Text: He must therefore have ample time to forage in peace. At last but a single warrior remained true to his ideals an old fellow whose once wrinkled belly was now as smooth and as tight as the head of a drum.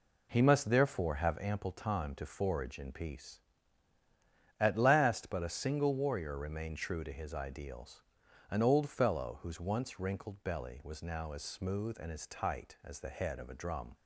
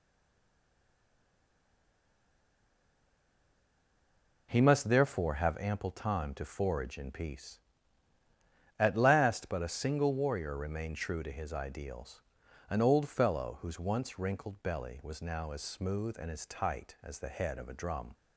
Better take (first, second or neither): first